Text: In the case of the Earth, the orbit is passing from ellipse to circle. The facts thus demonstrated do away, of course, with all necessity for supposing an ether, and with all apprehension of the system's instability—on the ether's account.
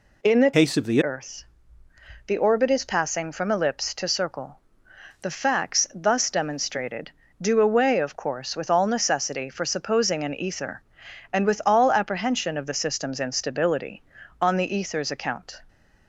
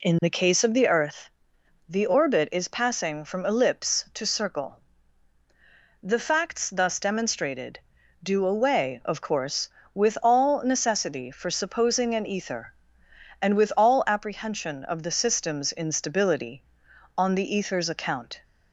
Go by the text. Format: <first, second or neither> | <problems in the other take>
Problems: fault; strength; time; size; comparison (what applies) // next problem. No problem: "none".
second | changes voice from "case" to "the"; from 0.5 to 1.0 s; 0.5 s long